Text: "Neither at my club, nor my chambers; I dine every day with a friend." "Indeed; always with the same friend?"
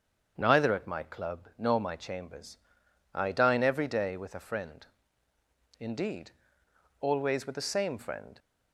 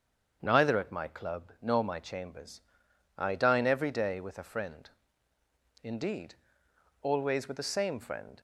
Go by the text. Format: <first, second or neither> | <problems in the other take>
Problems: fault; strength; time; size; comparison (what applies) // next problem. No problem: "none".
neither | starts louder than the rest; strong; the same in both